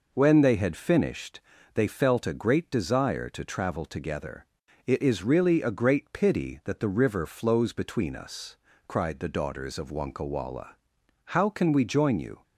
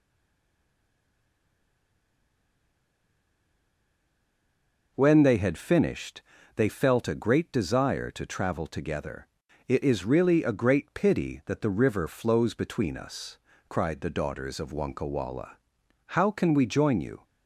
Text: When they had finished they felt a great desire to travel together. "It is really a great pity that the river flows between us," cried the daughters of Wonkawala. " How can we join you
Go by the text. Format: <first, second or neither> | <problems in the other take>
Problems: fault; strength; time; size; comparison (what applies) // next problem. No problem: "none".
first | stays silent before the first word; strong; until 4.9 s; 4.9 s long // pauses between "finished" and "they"; slight; at 6.2 s; 0.34 s long; slight in the first